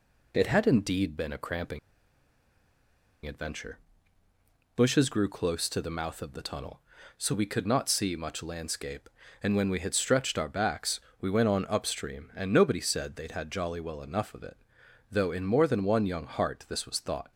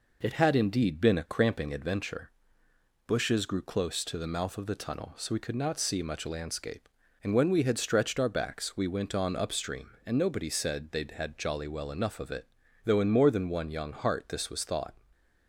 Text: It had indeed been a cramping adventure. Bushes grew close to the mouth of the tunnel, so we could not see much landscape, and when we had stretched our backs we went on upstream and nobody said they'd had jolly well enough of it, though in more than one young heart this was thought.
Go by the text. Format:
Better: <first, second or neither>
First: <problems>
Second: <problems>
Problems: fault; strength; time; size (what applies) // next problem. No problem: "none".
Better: second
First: pauses between "cramping" and "adventure"; strong; at 1.7 s; 1.4 s long // pauses between "backs" and "we"; slight; at 10.9 s; 0.22 s long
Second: none